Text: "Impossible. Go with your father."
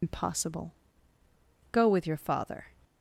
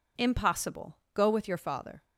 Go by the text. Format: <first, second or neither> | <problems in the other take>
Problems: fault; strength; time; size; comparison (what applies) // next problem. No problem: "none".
second | loses the start of "Impossible"; at 0.0 s; 90 ms